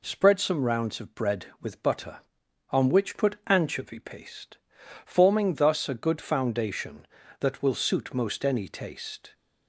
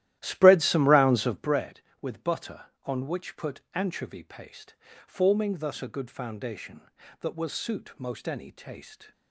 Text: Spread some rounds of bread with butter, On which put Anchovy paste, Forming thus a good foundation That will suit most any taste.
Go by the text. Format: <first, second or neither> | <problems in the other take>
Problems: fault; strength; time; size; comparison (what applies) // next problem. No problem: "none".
first | starts louder than the rest; strong; until 1.7 s; 13.5 dB